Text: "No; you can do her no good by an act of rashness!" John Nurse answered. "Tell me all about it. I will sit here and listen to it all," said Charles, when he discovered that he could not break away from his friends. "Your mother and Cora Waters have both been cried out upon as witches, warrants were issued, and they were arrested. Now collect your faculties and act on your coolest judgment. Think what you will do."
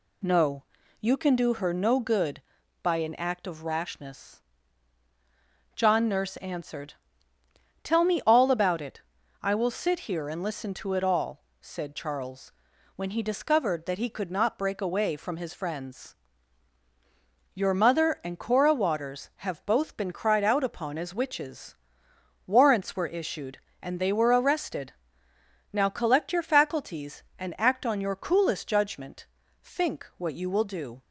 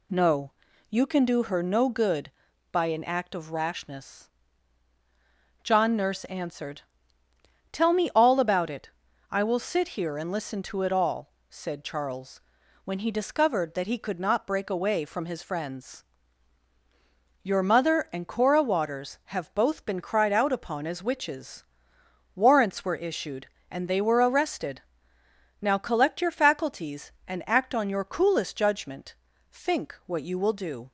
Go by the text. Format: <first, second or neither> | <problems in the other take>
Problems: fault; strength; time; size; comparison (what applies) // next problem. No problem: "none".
neither | none